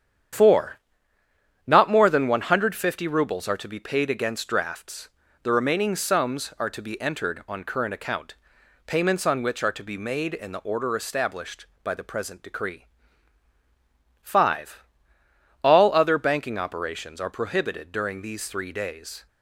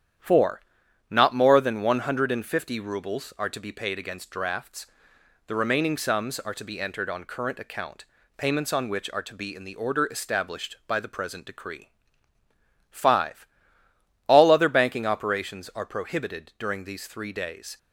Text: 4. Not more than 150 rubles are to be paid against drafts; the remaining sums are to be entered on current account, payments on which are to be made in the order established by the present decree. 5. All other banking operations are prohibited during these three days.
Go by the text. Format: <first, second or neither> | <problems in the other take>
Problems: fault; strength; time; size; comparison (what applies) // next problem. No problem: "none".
first | starts louder than the rest; strong; until 1.7 s; 9.5 dB; strong in the first // skips "made"; at 9.5 s